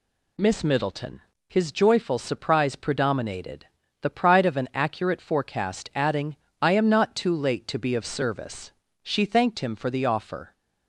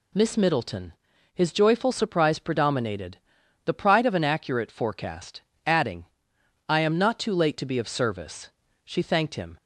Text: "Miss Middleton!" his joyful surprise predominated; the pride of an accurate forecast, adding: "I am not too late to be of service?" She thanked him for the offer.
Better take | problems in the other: first | stops before "for the offer"; at 9.5 s

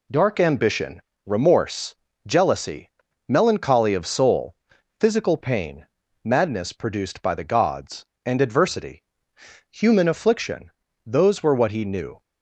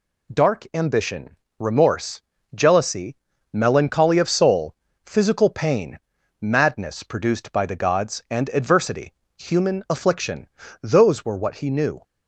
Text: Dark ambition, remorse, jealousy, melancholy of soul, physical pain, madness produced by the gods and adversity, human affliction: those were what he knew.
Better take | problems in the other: neither | none

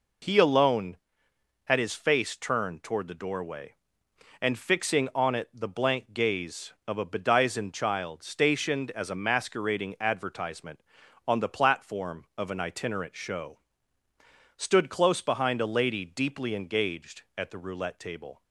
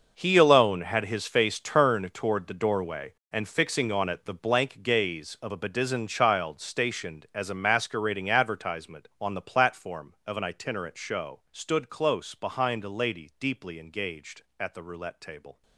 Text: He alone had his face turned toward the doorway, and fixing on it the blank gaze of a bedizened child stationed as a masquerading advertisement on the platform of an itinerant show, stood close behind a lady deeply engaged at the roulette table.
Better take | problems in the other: first | gets quieter; strong; throughout; 14 dB

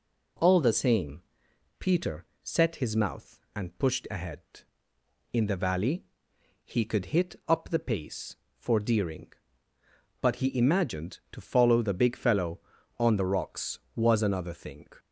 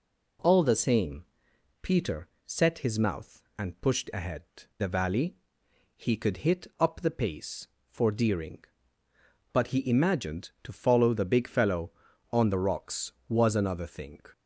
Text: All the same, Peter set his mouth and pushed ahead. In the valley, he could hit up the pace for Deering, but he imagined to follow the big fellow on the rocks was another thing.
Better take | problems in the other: first | pauses between "Peter" and "set"; slight; at 2.2 s; 0.20 s long; slight in the first // skips "In"; at 4.6 s

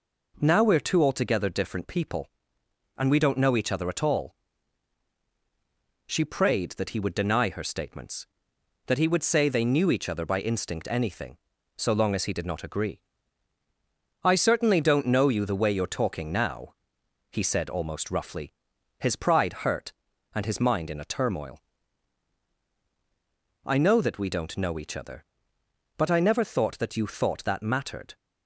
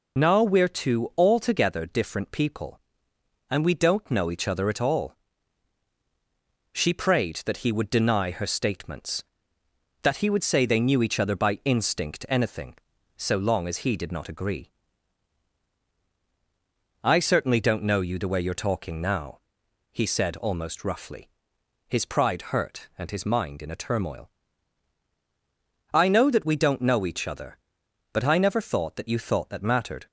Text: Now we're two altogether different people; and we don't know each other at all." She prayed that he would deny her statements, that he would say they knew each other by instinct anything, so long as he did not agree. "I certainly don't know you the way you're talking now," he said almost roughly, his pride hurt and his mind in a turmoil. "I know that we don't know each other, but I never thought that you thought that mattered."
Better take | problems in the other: first | loses the start of "Now"; at 0.1 s; 30 ms

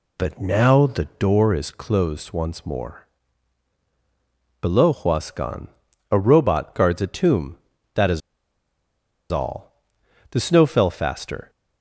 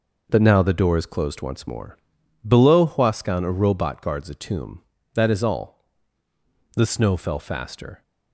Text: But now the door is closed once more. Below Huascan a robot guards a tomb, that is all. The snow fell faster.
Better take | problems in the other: second | pauses between "Huascan" and "a"; at 5.6 s; 0.44 s long // pauses between "is" and "all"; at 8.2 s; 1.1 s long

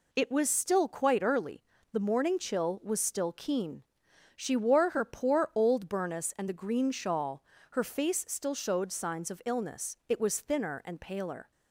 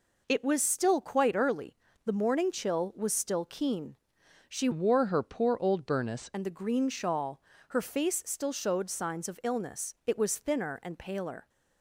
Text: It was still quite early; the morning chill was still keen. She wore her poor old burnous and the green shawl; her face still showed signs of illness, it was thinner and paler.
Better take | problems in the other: first | changes voice from "wore" to "burnous"; from 4.7 to 6.2 s; 1.5 s long

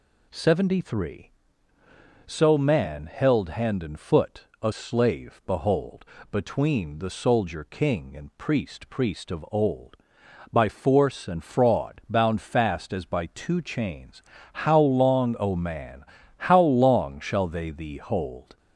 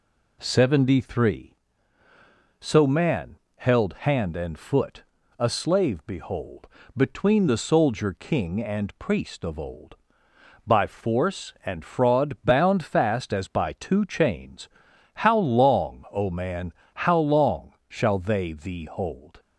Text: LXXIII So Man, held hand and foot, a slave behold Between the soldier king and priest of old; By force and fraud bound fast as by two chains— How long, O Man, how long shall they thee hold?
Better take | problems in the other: second | pauses between "behold" and "Between"; slight; at 6.0 s; 0.26 s long; slight in the second // says "priest" twice; at 8.8 s

